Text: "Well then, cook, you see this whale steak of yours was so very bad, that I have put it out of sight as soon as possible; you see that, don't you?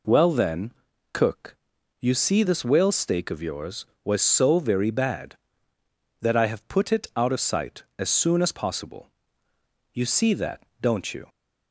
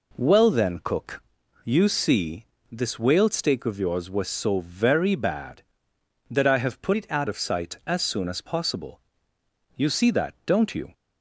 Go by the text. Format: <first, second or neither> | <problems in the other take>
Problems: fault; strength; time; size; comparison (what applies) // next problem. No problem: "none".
first | pauses between "see" and "this"; slight; at 2.4 s; 0.26 s long // changes voice from "it" to "out"; from 6.9 to 7.2 s; 0.3 s long